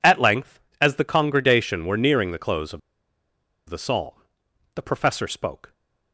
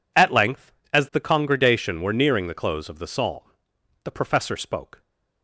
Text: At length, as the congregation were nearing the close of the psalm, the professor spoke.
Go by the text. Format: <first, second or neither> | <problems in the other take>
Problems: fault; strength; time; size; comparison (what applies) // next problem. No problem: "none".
second | pauses between "of" and "the"; noticeable; at 2.7 s; 0.87 s long